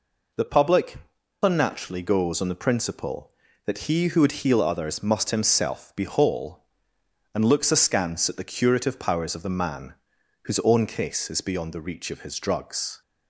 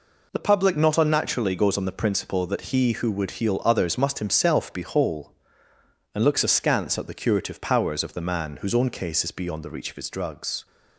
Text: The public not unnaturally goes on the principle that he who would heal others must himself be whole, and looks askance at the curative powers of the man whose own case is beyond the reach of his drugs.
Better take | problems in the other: second | skips "not"; at 1.1 s // pauses between "man" and "whose"; noticeable; at 9.9 s; 0.48 s long

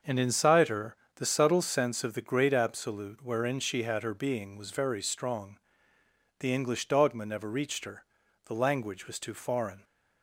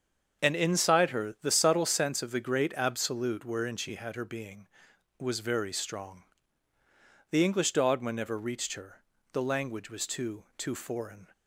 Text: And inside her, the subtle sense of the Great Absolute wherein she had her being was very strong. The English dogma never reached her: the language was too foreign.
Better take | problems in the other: first | starts louder than the rest; until 1.4 s; 7 dB; also in the first // says "too" twice; at 10.5 s

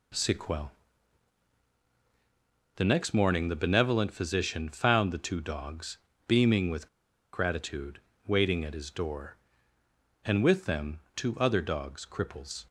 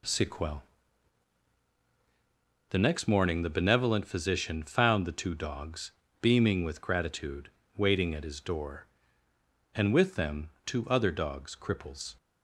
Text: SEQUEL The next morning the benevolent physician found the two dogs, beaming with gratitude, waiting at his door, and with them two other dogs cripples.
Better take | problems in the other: second | pauses between "SEQUEL" and "The"; strong; at 0.7 s; 2.0 s long; strong in the second // pauses between "with" and "gratitude"; noticeable; at 6.8 s; 0.46 s long

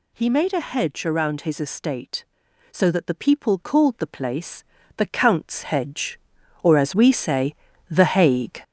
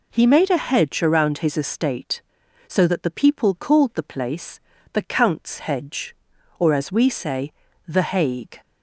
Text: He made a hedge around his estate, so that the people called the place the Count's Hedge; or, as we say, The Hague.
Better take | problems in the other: second | gets louder; noticeable; throughout; 4.5 dB // pauses between "place" and "the"; slight; at 4.6 s; 0.34 s long; slight in the second

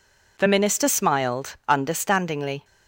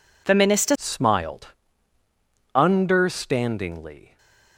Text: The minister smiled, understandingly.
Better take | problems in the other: first | changes voice at "smiled"; from 0.7 s on; 3.4 s long // stays silent after the last word; slight; from 4.0 s on; 0.5 s long

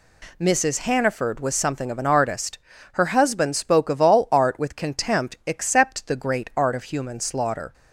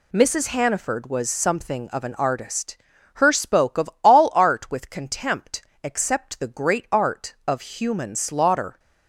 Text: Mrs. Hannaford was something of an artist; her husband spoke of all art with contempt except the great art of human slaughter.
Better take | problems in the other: first | skips "husband"; at 3.3 s // pauses between "contempt" and "except"; slight; at 5.6 s; 0.20 s long

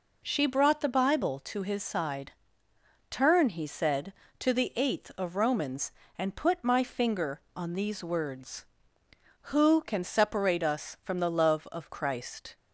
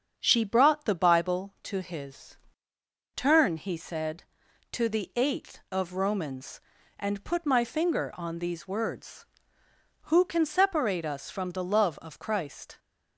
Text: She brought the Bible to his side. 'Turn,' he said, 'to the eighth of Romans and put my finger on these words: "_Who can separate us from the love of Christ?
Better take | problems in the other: first | starts louder than the rest; strong; until 1.1 s; 7 dB // skips "side"; at 2.7 s

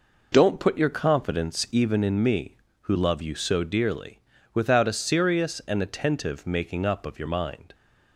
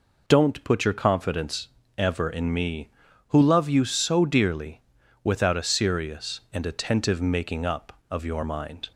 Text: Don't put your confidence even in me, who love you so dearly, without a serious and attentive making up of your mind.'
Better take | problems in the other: first | says "ever" for "even"; at 1.9 s

